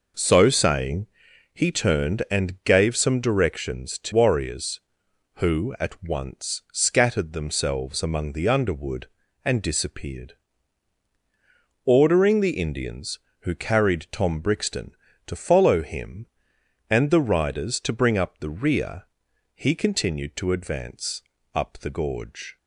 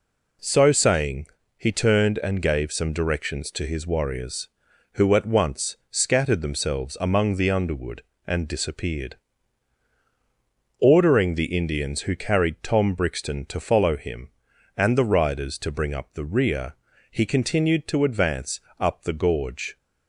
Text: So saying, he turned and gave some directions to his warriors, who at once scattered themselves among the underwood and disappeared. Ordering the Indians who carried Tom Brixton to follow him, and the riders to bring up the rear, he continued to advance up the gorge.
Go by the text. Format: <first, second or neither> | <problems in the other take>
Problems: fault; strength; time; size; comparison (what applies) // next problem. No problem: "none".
second | skips "his"; at 4.1 s // pauses between "advance" and "up"; slight; at 21.2 s; 0.32 s long; slight in the second